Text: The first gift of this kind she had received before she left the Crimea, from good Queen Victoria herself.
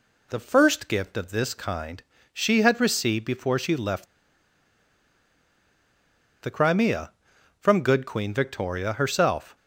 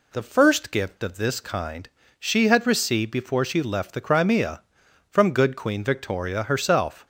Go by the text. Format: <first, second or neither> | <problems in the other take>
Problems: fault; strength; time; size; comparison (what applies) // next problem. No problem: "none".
second | pauses between "kind" and "she"; slight; at 2.0 s; 0.28 s long; slight in the second // pauses between "left" and "the"; strong; at 4.0 s; 2.3 s long